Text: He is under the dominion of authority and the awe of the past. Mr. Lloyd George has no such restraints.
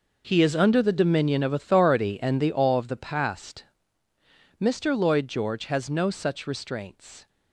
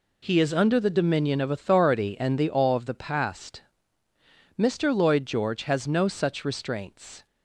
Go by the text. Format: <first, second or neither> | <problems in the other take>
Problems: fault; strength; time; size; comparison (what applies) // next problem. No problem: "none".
second | gets quieter; strong; throughout; 14 dB